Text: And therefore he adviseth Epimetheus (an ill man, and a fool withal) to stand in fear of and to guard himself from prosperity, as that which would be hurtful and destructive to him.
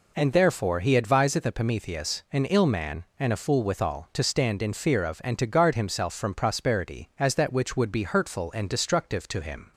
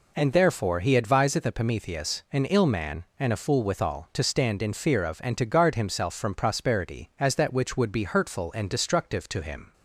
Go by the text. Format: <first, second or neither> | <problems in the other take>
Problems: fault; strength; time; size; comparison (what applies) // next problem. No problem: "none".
neither | none